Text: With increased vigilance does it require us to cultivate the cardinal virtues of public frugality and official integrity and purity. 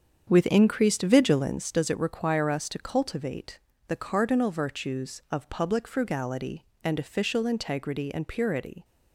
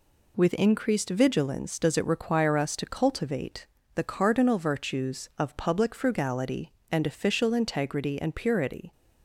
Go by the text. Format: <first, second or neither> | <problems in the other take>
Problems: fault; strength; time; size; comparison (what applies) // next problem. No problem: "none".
second | starts louder than the rest; strong; until 1.8 s; 7.5 dB // pauses between "cultivate" and "the"; slight; at 3.6 s; 0.26 s long; slight in the second